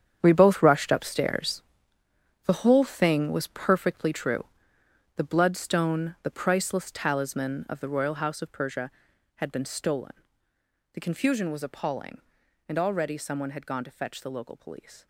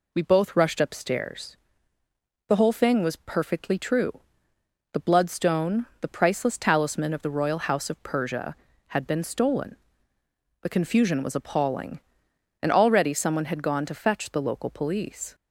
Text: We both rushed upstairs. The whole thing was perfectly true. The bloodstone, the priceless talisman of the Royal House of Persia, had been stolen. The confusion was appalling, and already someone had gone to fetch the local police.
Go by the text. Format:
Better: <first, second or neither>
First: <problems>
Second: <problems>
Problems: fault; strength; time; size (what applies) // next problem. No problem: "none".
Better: second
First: gets quieter; strong; throughout; 13.5 dB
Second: none